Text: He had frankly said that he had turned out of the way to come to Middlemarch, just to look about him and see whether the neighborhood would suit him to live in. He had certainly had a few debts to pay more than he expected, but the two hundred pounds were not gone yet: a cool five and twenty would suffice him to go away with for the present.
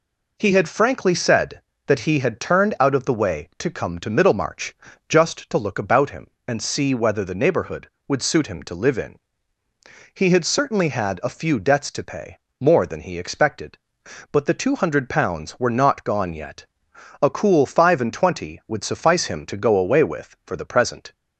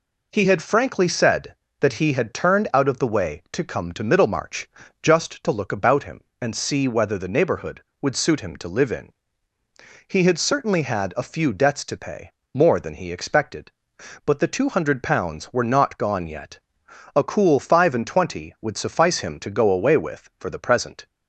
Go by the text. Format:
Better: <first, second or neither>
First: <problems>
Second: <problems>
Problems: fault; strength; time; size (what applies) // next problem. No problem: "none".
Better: neither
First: pauses between "pay" and "more"; slight; at 12.3 s; 0.22 s long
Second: pauses between "pay" and "more"; slight; at 12.3 s; 0.22 s long